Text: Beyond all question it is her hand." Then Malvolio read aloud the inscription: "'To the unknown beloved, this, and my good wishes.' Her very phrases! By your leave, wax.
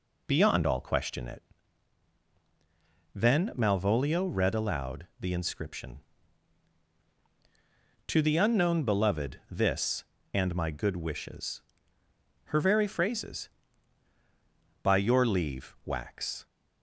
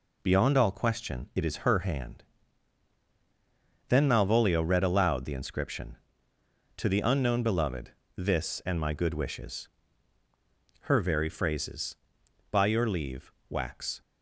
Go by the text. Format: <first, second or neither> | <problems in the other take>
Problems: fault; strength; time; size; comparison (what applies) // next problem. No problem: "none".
second | skips "is her hand"; at 2.2 s